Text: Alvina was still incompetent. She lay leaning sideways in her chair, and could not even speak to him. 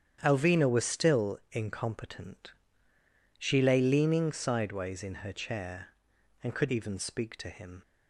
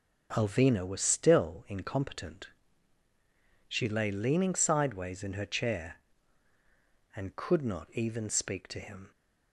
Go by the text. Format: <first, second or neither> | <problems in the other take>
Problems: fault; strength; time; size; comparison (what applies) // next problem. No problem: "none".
second | starts louder than the rest; strong; until 1.2 s; 9 dB // skips "not"; at 6.6 s